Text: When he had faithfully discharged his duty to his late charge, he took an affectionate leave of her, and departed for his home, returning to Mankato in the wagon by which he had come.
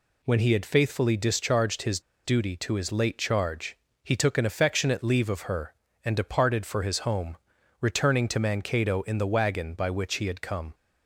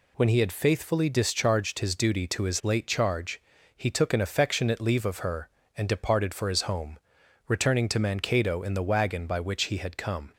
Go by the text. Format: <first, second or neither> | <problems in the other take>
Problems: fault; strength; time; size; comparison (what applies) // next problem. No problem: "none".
second | pauses between "his" and "duty"; slight; at 2.0 s; 0.24 s long